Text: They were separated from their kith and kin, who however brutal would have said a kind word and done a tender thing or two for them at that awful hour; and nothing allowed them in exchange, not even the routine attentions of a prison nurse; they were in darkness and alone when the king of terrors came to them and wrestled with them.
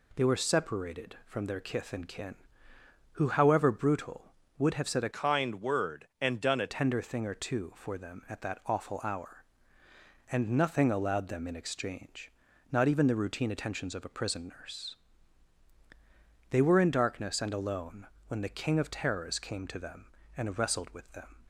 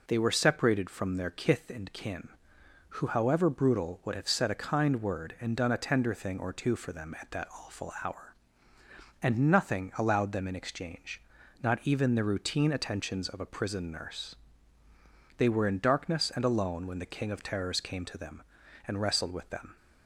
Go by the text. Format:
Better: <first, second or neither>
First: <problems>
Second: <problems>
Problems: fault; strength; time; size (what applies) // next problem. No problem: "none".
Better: second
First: changes voice from "kind" to "a"; from 5.1 to 6.6 s; 1.5 s long // pauses between "alone" and "when"; slight; at 18.0 s; 0.22 s long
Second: none